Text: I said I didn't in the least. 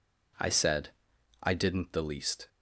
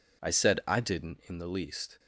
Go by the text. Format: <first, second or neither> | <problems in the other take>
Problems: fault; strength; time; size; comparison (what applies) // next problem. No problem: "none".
second | pauses between "said" and "I"; noticeable; at 0.8 s; 0.54 s long // skips "in"; at 1.9 s